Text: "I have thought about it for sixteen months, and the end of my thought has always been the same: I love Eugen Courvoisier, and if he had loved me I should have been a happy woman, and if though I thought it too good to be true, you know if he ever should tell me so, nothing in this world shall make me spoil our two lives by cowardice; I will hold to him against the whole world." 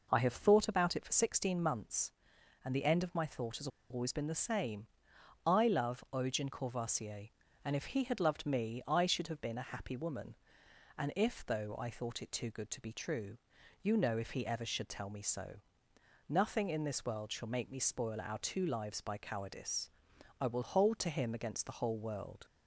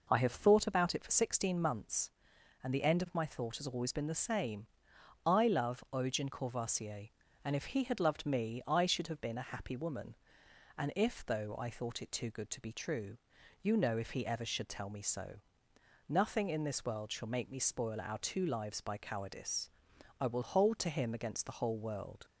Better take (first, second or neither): second